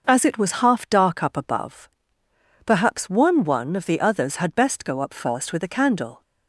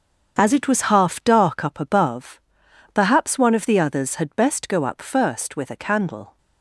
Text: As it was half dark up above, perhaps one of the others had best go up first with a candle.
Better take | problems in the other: second | starts louder than the rest; noticeable; until 1.0 s; 6 dB; strong in the second // says "one" twice; at 3.4 s

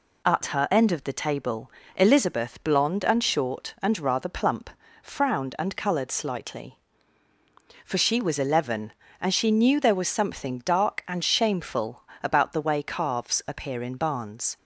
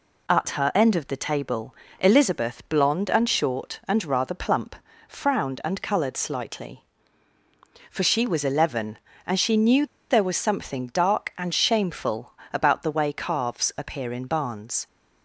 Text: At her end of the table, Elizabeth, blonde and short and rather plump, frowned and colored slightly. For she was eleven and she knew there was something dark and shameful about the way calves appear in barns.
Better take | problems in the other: first | pauses between "knew" and "there"; slight; at 9.8 s; 0.24 s long // pauses between "shameful" and "about"; slight; at 12.3 s; 0.20 s long; slight in the first

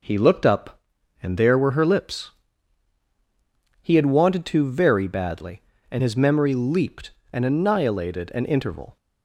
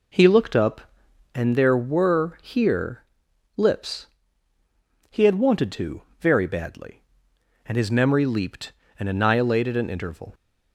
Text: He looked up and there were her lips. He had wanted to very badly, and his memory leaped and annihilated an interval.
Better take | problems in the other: first | says "here" for "her"; at 2.4 s // pauses between "to" and "very"; slight; at 6.0 s; 0.18 s long

